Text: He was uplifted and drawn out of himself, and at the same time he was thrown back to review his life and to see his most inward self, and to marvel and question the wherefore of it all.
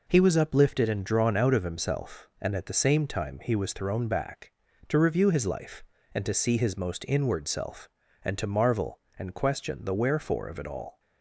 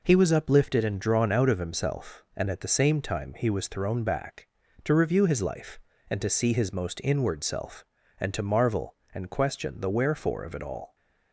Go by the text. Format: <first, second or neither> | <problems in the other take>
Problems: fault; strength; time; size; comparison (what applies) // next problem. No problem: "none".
neither | none